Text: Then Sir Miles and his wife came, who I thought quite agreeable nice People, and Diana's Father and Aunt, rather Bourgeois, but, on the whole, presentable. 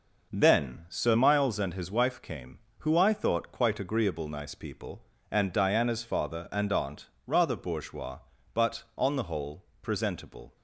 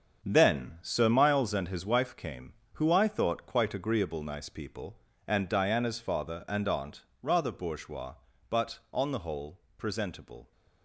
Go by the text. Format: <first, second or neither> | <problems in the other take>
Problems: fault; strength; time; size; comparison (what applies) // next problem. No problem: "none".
first | gets quieter; strong; throughout; 8.5 dB